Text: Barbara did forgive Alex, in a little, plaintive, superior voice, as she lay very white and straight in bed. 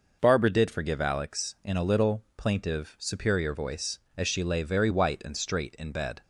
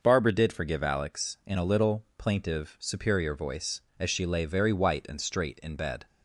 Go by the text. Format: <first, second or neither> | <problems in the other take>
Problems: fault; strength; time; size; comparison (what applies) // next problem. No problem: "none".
neither | none